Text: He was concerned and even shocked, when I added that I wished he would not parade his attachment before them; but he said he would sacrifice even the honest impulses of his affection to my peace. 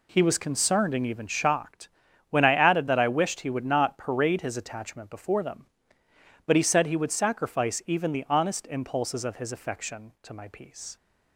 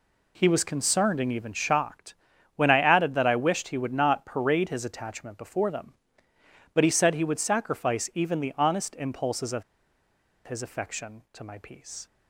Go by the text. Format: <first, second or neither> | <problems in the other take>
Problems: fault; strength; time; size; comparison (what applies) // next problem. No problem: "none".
first | pauses between "of" and "his"; noticeable; at 9.6 s; 0.82 s long